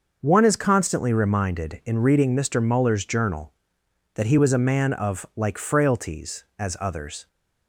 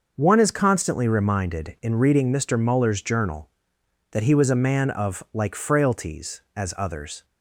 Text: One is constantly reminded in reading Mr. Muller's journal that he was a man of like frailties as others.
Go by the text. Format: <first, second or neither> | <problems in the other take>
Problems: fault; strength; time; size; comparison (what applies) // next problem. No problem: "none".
neither | starts louder than the rest; the same in both